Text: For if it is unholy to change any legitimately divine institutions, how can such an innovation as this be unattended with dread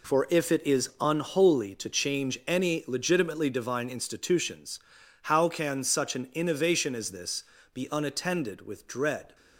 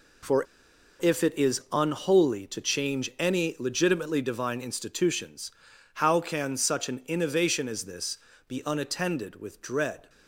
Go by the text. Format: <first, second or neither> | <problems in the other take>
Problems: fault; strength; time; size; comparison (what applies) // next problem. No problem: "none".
first | pauses between "For" and "if"; noticeable; at 0.4 s; 0.55 s long // pauses between "this" and "be"; slight; at 8.1 s; 0.28 s long; slight in the first